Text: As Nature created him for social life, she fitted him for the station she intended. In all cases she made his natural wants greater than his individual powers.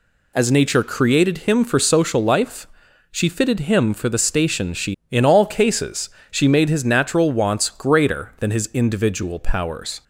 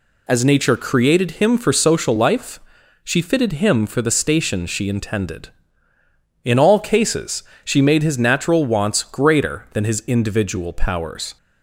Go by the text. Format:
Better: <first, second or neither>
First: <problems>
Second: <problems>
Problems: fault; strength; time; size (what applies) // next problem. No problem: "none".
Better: second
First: skips "intended"; at 5.0 s // pauses between "cases" and "she"; slight; at 6.0 s; 0.20 s long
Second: pauses between "cases" and "she"; slight; at 7.4 s; 0.20 s long